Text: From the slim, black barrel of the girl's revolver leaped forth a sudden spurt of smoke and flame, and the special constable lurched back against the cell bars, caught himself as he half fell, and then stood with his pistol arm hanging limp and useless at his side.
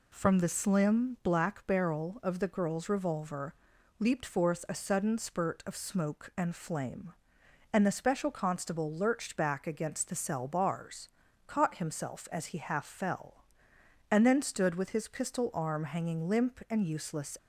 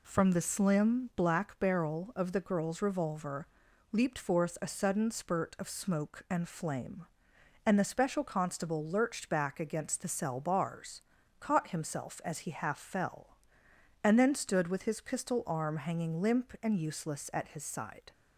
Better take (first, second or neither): second